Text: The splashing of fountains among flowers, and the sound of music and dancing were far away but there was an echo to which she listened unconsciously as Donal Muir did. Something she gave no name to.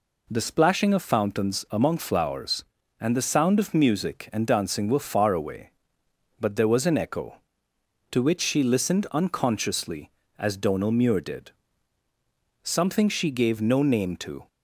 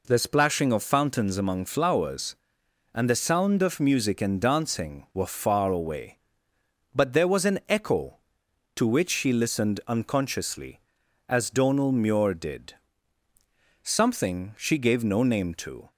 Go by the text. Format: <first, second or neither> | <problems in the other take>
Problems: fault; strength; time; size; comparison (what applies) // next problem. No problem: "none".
neither | none